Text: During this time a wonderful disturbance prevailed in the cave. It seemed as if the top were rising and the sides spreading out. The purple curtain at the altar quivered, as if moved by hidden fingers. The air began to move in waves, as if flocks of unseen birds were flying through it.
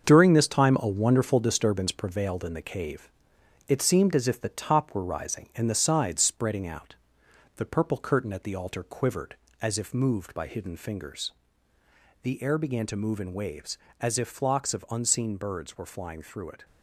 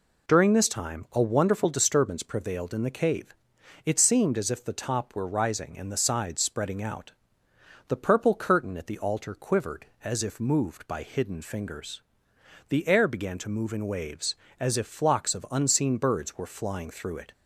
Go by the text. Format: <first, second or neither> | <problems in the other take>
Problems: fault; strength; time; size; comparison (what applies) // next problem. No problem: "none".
second | gets quieter; strong; throughout; 8 dB